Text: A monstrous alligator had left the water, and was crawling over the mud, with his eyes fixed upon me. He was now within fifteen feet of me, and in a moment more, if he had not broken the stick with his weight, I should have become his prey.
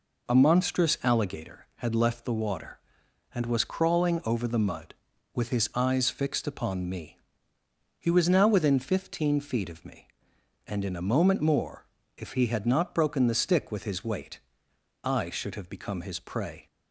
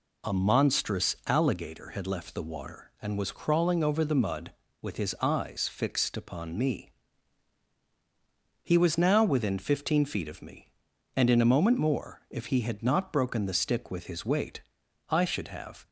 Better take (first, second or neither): first